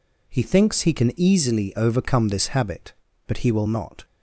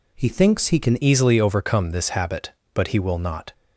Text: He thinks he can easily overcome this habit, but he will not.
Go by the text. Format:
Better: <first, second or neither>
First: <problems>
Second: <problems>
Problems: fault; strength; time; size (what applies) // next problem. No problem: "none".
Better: first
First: none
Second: changes voice at "easily"; from 1.0 s on; 2.5 s long